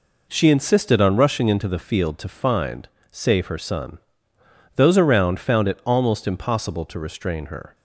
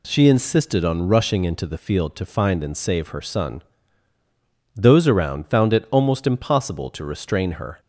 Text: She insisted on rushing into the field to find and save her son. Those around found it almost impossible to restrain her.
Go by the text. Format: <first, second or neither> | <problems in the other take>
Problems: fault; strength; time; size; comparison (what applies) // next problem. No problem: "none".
second | skips "and"; at 2.9 s